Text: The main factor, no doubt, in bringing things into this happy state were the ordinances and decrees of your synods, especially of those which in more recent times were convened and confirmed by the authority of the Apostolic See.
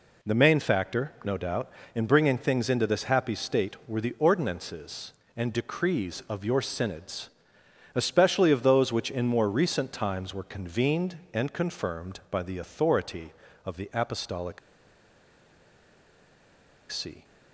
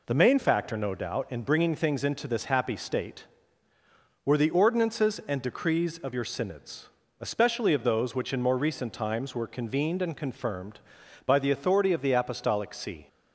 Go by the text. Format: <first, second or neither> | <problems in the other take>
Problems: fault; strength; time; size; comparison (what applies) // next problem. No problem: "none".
second | pauses between "Apostolic" and "See"; strong; at 14.5 s; 2.3 s long